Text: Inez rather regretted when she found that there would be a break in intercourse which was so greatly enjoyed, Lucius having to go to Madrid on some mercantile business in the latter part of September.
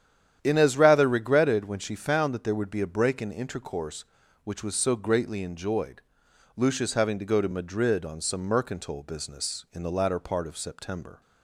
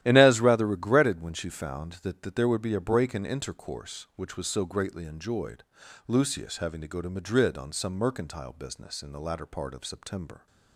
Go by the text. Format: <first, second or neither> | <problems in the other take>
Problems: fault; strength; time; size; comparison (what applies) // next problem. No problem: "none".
first | starts louder than the rest; strong; until 1.0 s; 13 dB; strong in the first // says "that" twice; at 2.2 s